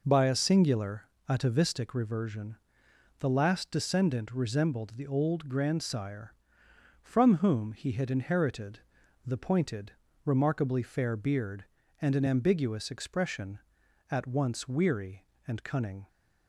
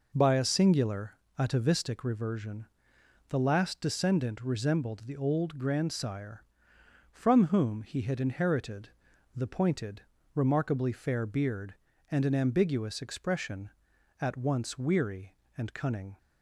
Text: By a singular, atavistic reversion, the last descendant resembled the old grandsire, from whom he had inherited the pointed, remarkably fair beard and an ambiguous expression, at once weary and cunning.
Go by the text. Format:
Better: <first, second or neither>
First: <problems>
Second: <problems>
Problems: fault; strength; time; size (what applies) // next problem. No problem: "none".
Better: neither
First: pauses between "inherited" and "the"; at 8.8 s; 0.44 s long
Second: pauses between "inherited" and "the"; at 8.9 s; 0.44 s long